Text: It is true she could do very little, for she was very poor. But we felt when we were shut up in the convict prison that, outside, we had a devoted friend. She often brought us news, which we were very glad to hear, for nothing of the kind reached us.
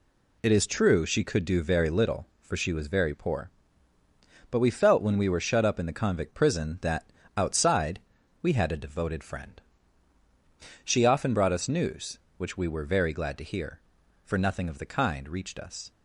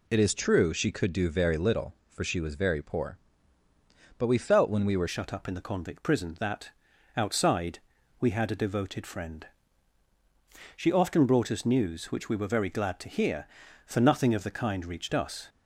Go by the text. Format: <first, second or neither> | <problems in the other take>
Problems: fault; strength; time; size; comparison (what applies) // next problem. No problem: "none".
first | changes voice at "shut"; from 5.0 s on; 10.4 s long